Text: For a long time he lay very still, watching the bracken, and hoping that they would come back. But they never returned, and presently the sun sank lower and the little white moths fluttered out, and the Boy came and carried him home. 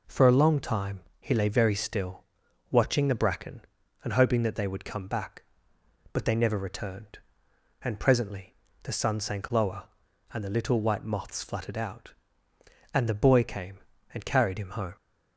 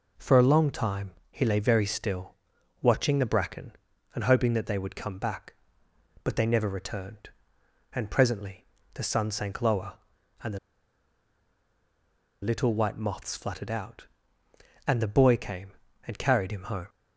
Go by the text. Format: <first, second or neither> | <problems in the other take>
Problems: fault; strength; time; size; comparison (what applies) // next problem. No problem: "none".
first | pauses between "time" and "he"; slight; at 1.1 s; 0.18 s long; slight in the first // pauses between "presently" and "the"; slight; at 8.6 s; 0.28 s long; slight in the first // pauses between "the" and "little"; strong; at 10.5 s; 1.8 s long